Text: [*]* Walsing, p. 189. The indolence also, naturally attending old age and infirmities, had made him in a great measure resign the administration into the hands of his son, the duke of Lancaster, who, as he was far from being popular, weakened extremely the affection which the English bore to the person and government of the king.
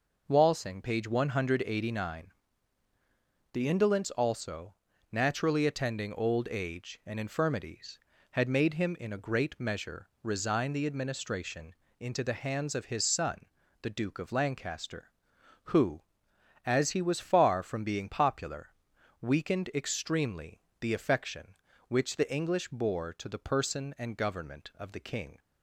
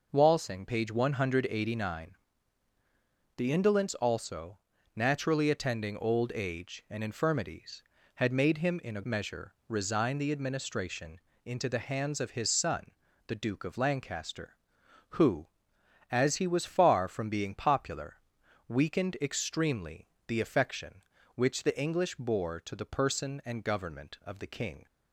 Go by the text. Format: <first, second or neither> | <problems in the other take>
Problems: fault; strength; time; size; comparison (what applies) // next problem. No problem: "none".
first | skips "great"; at 9.0 s // pauses between "measure" and "resign"; slight; at 9.5 s; 0.16 s long; slight in the first // pauses between "administration" and "into"; slight; at 11.2 s; 0.24 s long; slight in the first // pauses between "extremely" and "the"; slight; at 20.0 s; 0.22 s long; slight in the first